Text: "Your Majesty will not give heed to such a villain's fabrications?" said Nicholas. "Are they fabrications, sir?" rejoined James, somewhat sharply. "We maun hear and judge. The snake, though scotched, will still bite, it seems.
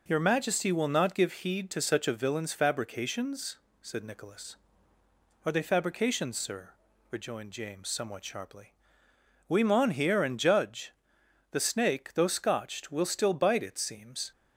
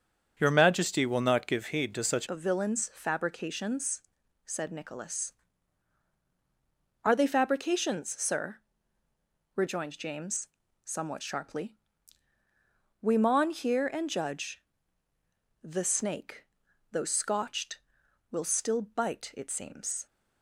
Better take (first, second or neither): first